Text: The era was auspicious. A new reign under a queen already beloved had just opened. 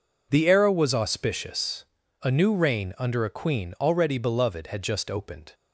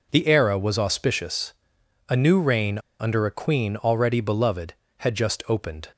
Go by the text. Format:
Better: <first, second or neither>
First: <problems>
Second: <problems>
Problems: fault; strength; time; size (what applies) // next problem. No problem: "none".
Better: first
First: none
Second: pauses between "reign" and "under"; slight; at 2.7 s; 0.20 s long